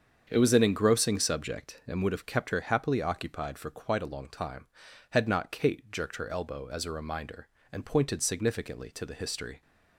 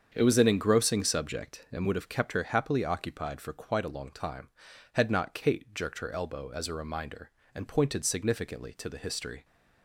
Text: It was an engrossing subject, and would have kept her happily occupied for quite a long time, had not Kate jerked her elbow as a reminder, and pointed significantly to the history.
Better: neither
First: starts louder than the rest; strong; until 1.3 s; 7 dB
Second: starts louder than the rest; strong; until 1.1 s; 7 dB

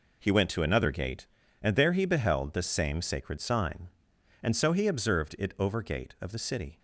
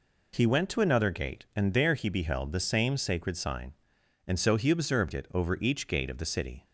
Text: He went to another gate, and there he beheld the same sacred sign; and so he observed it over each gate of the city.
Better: second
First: skips "each"; at 5.8 s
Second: none

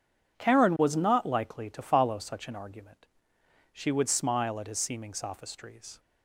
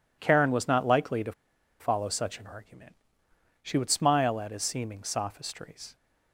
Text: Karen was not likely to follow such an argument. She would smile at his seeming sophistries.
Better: first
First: none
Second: pauses between "to" and "follow"; noticeable; at 1.3 s; 0.48 s long

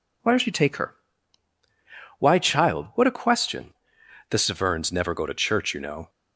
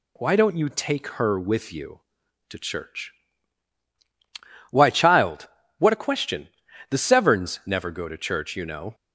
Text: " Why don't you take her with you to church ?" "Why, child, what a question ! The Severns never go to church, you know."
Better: second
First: skips "with you to church"; at 1.2 s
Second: none

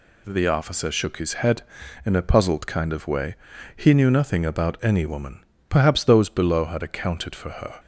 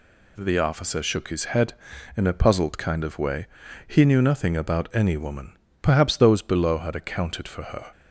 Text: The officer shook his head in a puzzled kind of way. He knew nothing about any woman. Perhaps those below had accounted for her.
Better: neither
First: none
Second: none

